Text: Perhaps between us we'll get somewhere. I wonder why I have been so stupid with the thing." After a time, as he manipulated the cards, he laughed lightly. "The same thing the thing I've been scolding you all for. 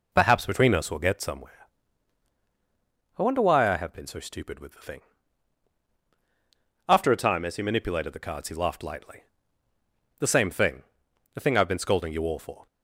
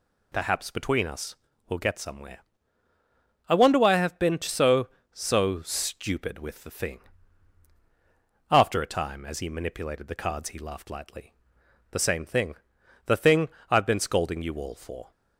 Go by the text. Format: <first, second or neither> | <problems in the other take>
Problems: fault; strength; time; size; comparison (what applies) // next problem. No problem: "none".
first | pauses between "us" and "we'll"; slight; at 1.3 s; 0.34 s long // says "so" twice; at 5.1 s // pauses between "thing" and "the"; noticeable; at 12.5 s; 0.50 s long; noticeable in the first // pauses between "thing" and "I've"; slight; at 13.4 s; 0.20 s long